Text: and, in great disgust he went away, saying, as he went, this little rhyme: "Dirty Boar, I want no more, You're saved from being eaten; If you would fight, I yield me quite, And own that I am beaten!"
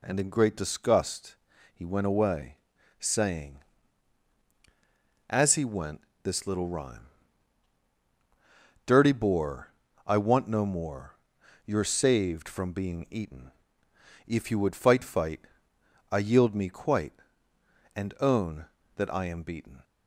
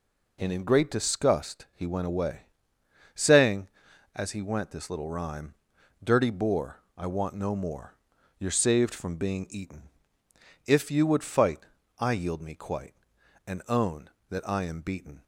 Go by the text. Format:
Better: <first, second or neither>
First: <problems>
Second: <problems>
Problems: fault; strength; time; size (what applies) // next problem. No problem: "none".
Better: second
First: pauses between "disgust" and "he"; at 1.3 s; 0.38 s long // says "fight" twice; at 15.0 s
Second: none